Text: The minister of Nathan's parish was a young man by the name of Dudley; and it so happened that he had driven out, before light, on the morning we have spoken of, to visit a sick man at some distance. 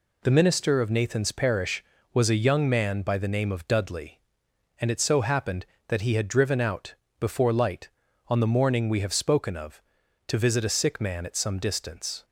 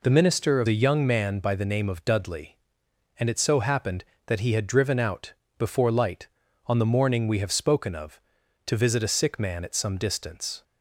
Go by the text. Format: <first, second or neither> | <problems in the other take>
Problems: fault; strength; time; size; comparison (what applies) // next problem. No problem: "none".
first | skips "Nathan's parish was"; at 0.6 s